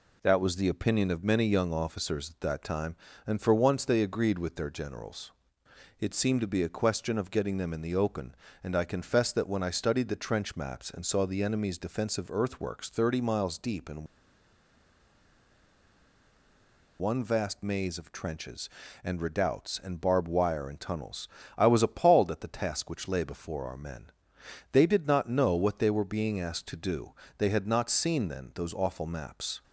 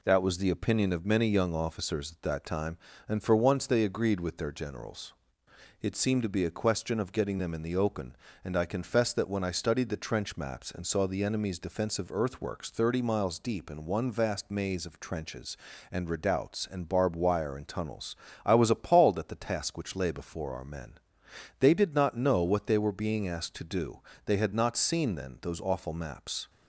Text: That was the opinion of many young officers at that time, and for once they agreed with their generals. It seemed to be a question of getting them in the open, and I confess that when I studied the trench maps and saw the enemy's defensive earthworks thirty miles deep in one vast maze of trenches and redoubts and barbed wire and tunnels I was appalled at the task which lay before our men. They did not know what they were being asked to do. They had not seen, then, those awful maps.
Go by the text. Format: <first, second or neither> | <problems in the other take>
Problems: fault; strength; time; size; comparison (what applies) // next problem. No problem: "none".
second | pauses between "in" and "one"; strong; at 14.0 s; 2.9 s long // pauses between "tunnels" and "I"; slight; at 21.2 s; 0.30 s long; slight in the second